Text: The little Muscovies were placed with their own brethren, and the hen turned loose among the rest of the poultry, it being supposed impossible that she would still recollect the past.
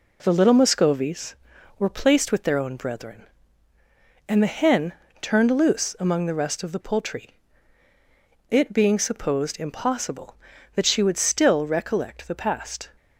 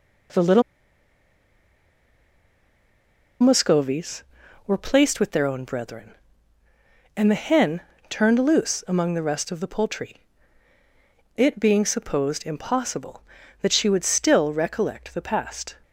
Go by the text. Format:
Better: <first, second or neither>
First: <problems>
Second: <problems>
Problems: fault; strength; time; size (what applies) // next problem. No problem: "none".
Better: first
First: pauses between "hen" and "turned"; slight; at 4.9 s; 0.26 s long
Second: pauses between "little" and "Muscovies"; strong; at 0.6 s; 2.7 s long // pauses between "hen" and "turned"; slight; at 7.8 s; 0.26 s long